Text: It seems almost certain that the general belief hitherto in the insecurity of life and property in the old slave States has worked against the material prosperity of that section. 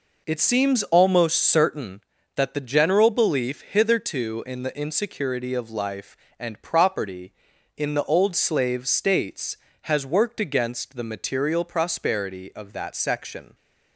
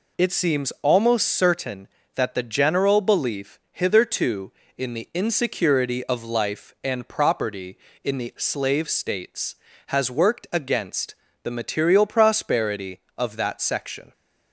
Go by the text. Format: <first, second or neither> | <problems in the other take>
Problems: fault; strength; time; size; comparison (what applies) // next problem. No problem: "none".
first | skips "old"; at 8.3 s // pauses between "against" and "the"; slight; at 11.1 s; 0.30 s long